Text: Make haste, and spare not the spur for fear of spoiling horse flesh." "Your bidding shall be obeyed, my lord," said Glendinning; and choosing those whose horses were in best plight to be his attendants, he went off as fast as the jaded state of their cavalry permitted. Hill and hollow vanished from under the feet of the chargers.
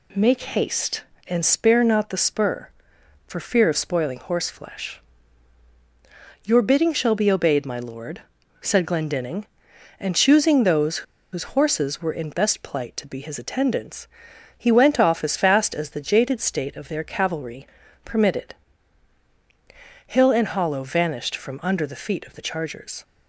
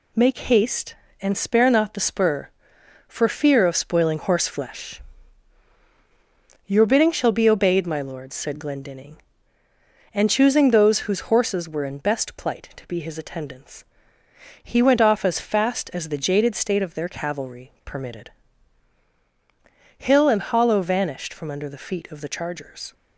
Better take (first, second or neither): second